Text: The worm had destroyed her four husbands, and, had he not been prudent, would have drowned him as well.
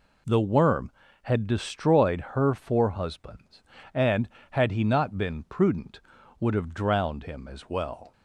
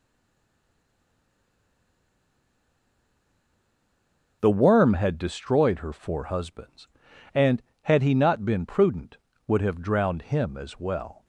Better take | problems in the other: first | stays silent before the first word; strong; until 4.4 s; 4.4 s long

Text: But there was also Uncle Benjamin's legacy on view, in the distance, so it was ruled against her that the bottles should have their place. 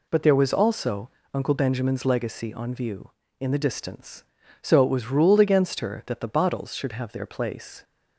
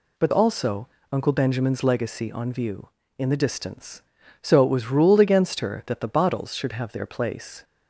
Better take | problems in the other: first | skips "there was"; at 0.3 s // pauses between "also" and "Uncle"; slight; at 0.8 s; 0.24 s long; slight in the first

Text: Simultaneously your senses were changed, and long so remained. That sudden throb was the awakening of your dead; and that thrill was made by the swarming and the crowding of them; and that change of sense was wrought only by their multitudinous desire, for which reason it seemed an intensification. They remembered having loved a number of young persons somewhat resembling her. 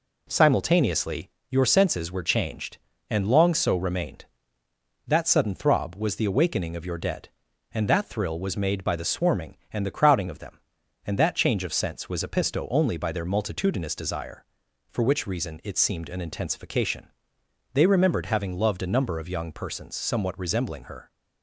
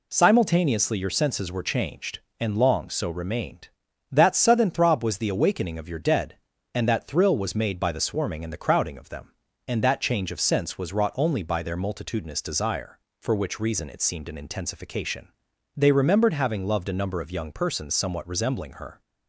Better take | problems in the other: second | pauses between "Simultaneously" and "your"; slight; at 1.3 s; 0.20 s long // says "episto" for "wrought"; at 12.2 s

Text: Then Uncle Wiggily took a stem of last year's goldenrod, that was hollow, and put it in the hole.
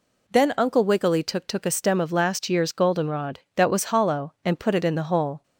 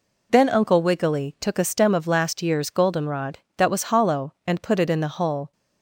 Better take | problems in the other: second | says "took" twice; at 1.4 s

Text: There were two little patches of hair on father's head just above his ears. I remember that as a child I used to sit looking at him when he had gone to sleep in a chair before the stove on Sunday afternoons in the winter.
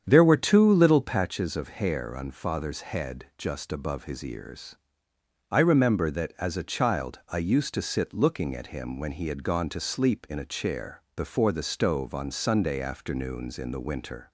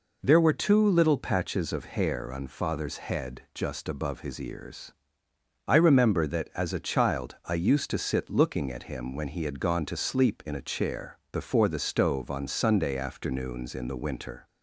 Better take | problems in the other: second | starts louder than the rest; strong; until 1.3 s; 8.5 dB // pauses between "chair" and "before"; slight; at 10.9 s; 0.16 s long; slight in the second

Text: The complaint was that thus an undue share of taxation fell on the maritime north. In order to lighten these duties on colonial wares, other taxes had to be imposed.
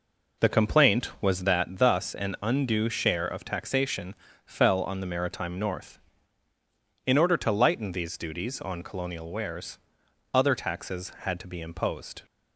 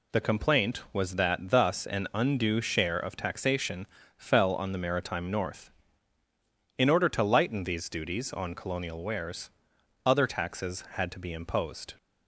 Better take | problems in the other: second | starts louder than the rest; noticeable; until 1.7 s; 4.5 dB // pauses between "taxation" and "fell"; slight; at 4.1 s; 0.30 s long; slight in the second

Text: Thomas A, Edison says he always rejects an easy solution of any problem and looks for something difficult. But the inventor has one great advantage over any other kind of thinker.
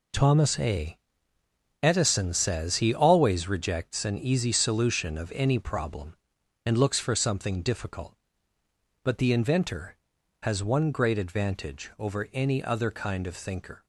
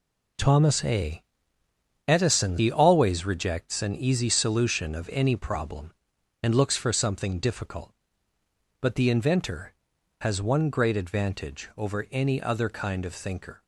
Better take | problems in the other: first | skips "says"; at 2.5 s

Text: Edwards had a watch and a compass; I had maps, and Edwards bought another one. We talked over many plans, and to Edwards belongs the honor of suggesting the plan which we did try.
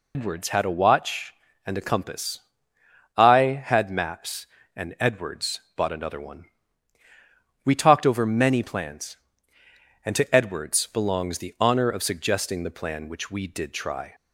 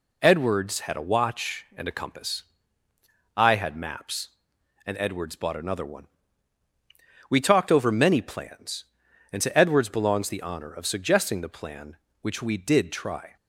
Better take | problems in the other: second | loses the start of "Edwards"; at 0.1 s; 120 ms

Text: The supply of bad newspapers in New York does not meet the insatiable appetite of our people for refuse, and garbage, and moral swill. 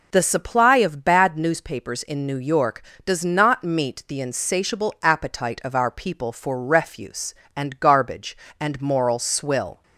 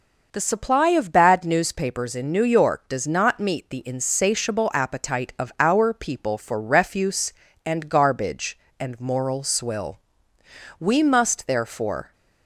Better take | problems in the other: first | goes on to say "We must therefore"; from 10.7 s on; 1.3 s long

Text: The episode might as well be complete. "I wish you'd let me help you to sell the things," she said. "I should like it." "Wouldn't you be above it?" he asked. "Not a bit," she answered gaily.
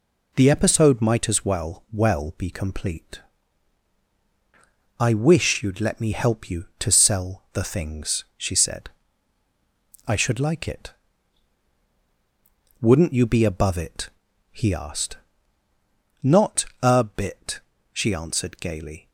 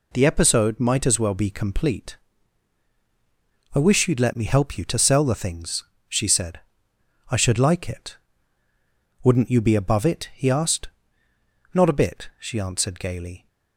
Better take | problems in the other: second | says "well" twice; at 1.9 s // pauses between "Not" and "a"; slight; at 16.6 s; 0.18 s long

